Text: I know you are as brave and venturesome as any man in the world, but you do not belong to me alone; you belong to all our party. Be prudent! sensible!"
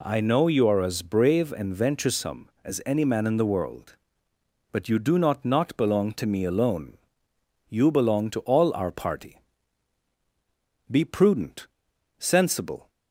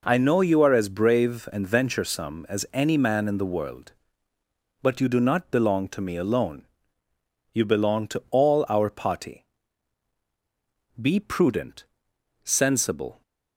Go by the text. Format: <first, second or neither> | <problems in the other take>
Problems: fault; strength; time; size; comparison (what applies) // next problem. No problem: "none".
second | says "not" twice; at 5.4 s